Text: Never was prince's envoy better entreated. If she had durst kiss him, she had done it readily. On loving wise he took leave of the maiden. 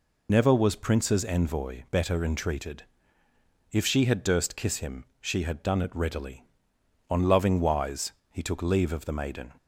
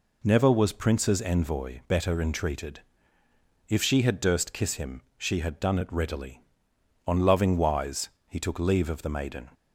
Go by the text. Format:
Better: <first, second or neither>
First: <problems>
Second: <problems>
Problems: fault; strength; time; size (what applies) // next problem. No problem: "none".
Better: second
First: loses the start of "Never"; at 0.2 s; 30 ms // pauses between "wise" and "he"; slight; at 8.1 s; 0.18 s long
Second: pauses between "wise" and "he"; slight; at 8.0 s; 0.18 s long